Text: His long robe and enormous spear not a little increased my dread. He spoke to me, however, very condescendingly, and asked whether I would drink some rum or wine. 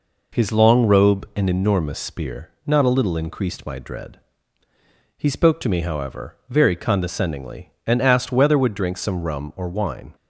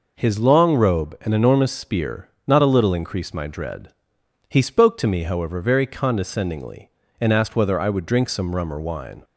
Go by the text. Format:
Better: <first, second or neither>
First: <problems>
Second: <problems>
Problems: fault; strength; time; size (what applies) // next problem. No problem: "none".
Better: second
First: pauses between "spear" and "not"; slight; at 2.4 s; 0.15 s long // skips "I"; at 8.5 s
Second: pauses between "spear" and "not"; slight; at 2.2 s; 0.18 s long